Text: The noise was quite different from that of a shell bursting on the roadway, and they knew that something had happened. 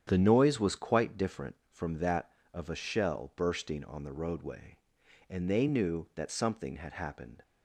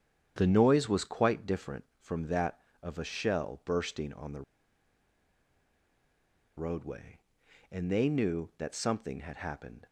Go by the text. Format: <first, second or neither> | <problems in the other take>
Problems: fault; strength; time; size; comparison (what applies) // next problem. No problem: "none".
first | starts louder than the rest; strong; until 1.3 s; 9 dB; strong in the first // pauses between "the" and "roadway"; strong; at 4.4 s; 2.1 s long